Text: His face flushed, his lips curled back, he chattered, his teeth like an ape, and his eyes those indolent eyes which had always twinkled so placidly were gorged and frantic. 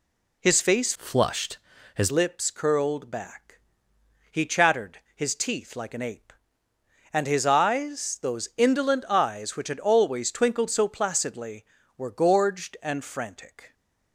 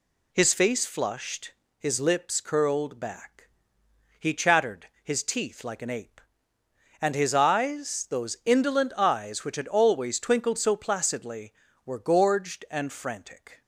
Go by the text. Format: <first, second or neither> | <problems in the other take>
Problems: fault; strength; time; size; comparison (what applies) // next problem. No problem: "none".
second | changes voice from "flushed" to "his"; from 0.9 to 2.1 s; 1.2 s long